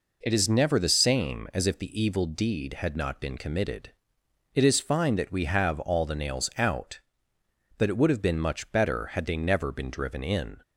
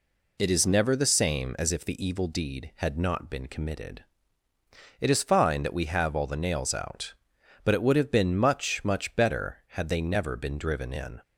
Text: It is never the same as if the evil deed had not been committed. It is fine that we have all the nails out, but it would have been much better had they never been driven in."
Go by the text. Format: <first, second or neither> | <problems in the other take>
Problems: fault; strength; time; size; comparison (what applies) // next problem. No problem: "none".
first | says "much" twice; at 8.8 s